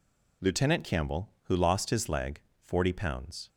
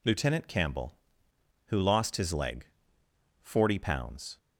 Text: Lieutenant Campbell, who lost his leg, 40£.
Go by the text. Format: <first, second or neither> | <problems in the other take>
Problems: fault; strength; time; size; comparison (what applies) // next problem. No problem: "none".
neither | none